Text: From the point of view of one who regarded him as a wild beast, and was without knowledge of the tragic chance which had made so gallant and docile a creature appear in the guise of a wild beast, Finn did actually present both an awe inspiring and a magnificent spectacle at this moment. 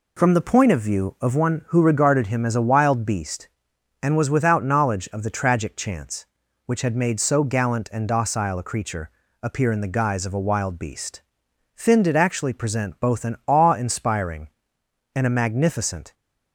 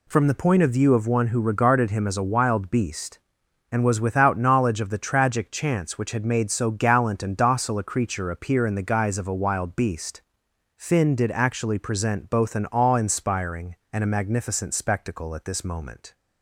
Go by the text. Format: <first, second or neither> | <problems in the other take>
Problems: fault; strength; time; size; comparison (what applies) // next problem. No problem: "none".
second | pauses between "creature" and "appear"; slight; at 9.1 s; 0.32 s long // stops before "spectacle at this moment"; at 16.1 s